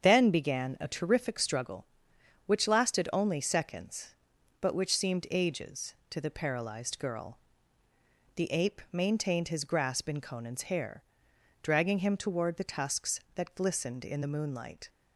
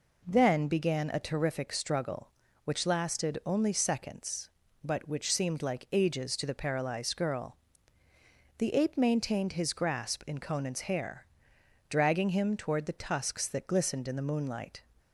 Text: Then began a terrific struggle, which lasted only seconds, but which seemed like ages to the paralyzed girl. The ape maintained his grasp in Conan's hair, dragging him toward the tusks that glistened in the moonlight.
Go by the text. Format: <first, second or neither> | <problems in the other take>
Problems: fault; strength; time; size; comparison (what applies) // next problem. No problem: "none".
second | starts louder than the rest; strong; until 1.0 s; 7 dB // skips "like"; at 5.2 s